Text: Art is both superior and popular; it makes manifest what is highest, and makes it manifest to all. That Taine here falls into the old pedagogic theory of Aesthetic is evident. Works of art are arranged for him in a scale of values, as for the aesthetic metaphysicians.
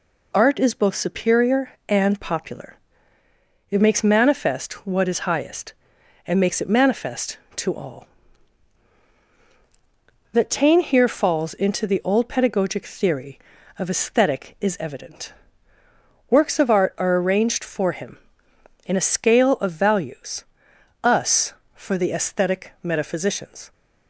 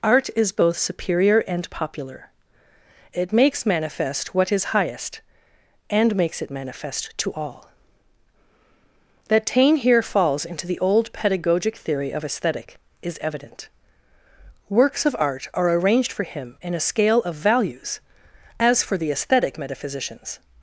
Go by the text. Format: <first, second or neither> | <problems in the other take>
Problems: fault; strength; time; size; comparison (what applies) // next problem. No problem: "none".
second | says "us" for "as"; at 21.0 s